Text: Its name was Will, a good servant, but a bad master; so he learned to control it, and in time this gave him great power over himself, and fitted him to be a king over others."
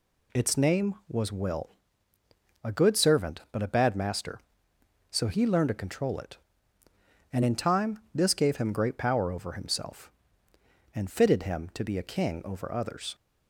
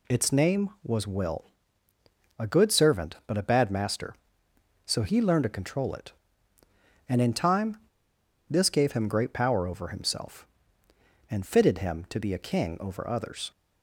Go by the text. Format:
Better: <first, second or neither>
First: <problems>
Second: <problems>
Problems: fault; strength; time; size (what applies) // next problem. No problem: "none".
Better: first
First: none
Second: pauses between "time" and "this"; noticeable; at 7.7 s; 0.71 s long